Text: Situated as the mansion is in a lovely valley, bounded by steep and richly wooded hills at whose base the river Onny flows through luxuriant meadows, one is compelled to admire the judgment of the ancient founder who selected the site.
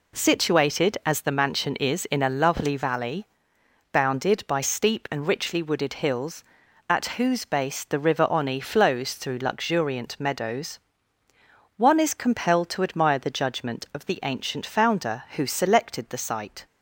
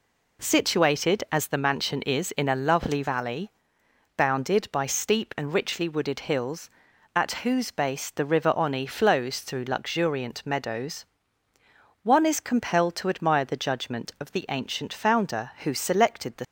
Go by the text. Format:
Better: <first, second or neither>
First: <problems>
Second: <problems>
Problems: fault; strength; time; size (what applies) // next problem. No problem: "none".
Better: first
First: none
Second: stops before "site"; at 16.4 s